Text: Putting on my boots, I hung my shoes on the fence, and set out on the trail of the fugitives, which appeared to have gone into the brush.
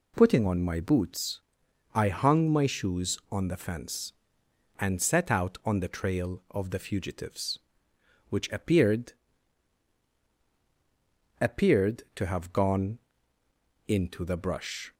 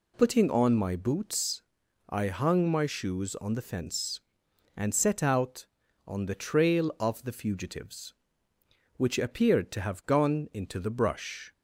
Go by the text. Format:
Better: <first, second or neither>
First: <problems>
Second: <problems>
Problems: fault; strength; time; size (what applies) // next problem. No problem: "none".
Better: second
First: says "appeared" twice; at 11.4 s // pauses between "gone" and "into"; noticeable; at 12.9 s; 0.88 s long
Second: none